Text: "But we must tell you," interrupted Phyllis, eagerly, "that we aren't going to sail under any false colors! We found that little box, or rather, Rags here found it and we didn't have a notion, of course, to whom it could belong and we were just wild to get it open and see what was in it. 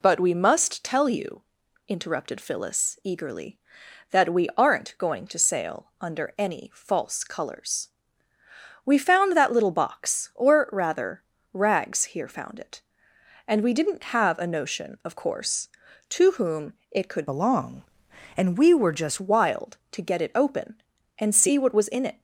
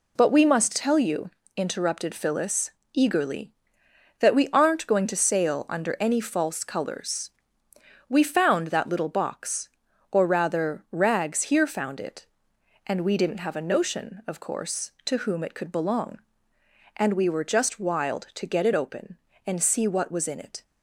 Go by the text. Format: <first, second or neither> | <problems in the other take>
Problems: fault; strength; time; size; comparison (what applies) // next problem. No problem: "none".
second | pauses between "whom" and "it"; slight; at 16.7 s; 0.16 s long // changes voice from "belong" to "just"; from 17.2 to 19.1 s; 1.9 s long